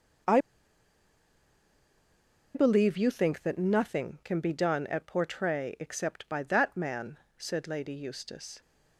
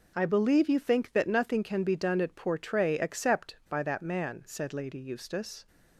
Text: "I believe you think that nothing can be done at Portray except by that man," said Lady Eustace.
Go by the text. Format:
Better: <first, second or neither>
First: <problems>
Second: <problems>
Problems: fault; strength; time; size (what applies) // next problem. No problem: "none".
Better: second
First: pauses between "I" and "believe"; strong; at 0.3 s; 2.1 s long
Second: none